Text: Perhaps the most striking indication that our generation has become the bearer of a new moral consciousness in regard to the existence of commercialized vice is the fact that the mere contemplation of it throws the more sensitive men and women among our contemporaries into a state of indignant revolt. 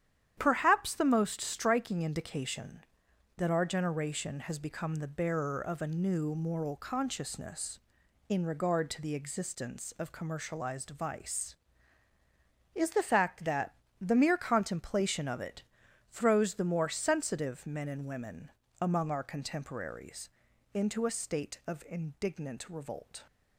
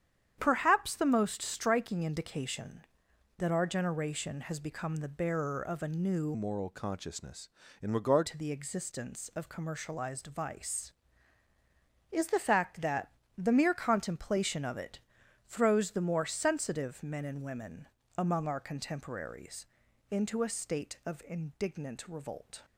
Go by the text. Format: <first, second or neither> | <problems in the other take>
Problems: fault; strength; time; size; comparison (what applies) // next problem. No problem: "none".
first | starts louder than the rest; strong; until 1.4 s; 9 dB; strong in the first // changes voice from "moral" to "regard"; from 6.3 to 8.2 s; 1.9 s long // pauses between "that" and "the"; slight; at 13.0 s; 0.26 s long; slight in the first // pauses between "it" and "throws"; noticeable; at 14.9 s; 0.48 s long; noticeable in the first // pauses between "women" and "among"; slight; at 17.8 s; 0.28 s long; slight in the first // pauses between "contemporaries" and "into"; at 19.6 s; 0.42 s long; also in the first